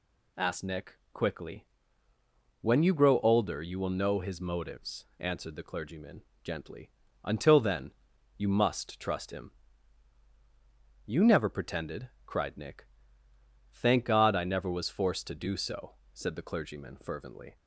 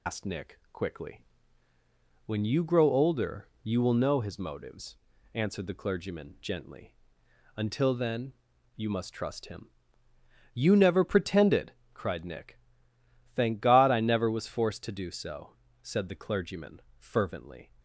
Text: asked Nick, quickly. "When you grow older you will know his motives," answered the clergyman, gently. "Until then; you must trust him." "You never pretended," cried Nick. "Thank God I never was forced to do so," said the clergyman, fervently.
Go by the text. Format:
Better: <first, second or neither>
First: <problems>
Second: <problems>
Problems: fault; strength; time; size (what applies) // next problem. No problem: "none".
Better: first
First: none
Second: loses the start of "asked"; at 0.0 s; 90 ms